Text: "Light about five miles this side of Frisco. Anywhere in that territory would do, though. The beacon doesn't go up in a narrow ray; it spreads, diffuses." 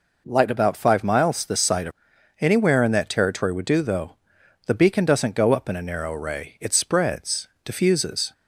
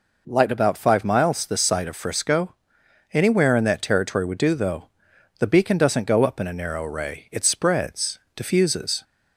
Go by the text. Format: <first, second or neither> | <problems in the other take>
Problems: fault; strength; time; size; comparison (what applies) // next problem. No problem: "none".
second | skips "Frisco"; at 2.1 s